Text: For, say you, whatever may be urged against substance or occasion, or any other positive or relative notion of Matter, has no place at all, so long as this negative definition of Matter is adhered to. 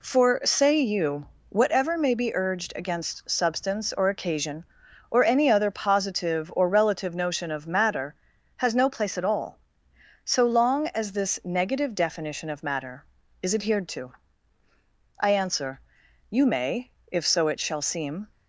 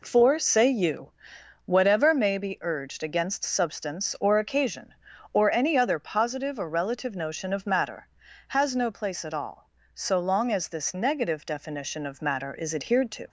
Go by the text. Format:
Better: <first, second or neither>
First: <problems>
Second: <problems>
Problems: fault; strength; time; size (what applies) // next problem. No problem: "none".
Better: second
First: goes on to say "I answer you may if so it shall seem"; strong; from 15.1 s on; 3.0 s long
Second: none